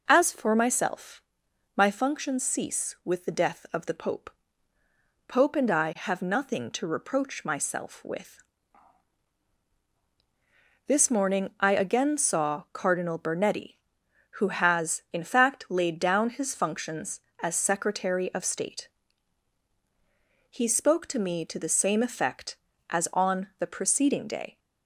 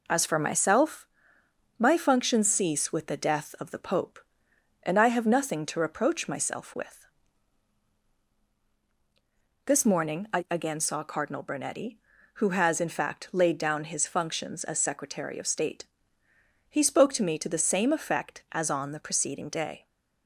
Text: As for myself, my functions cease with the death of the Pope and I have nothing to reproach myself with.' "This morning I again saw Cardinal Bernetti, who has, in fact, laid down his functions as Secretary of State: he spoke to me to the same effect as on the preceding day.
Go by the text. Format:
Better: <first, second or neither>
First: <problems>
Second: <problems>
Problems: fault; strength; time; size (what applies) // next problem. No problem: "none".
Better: second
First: says "Pope" twice; at 5.2 s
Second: none